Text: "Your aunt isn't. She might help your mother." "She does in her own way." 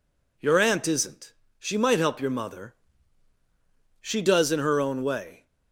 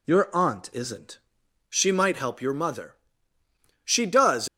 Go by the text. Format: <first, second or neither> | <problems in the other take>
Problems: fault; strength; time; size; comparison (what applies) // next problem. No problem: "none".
first | stops before "in her own way"; at 4.4 s